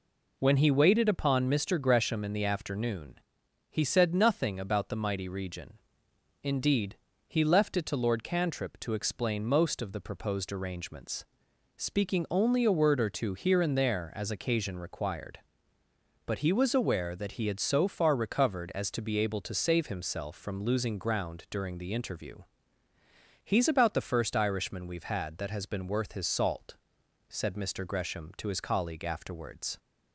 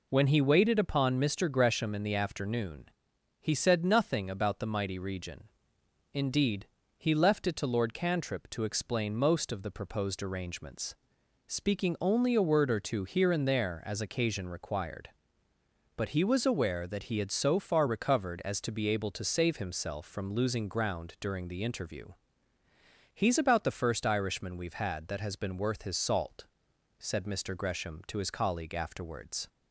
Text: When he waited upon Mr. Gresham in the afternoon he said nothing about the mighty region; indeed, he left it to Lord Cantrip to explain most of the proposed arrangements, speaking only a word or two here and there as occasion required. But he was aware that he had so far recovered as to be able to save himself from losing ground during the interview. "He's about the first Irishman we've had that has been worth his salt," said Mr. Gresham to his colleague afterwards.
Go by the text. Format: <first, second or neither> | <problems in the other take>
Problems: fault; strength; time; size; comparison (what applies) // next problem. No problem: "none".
neither | pauses between "afternoon" and "he"; noticeable; the same in both